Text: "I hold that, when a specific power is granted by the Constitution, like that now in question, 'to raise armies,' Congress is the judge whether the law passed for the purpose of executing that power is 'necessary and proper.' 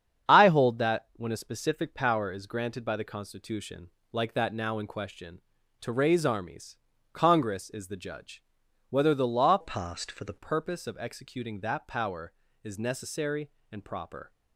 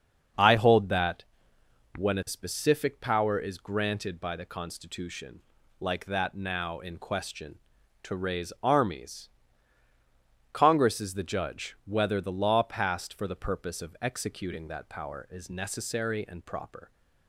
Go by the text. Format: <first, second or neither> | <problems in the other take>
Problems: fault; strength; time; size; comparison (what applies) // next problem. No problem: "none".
second | starts louder than the rest; strong; until 1.3 s; 8 dB; also in the second // pauses between "judge" and "whether"; noticeable; at 8.4 s; 0.48 s long // changes voice from "passed" to "the"; from 9.6 to 10.3 s; 0.7 s long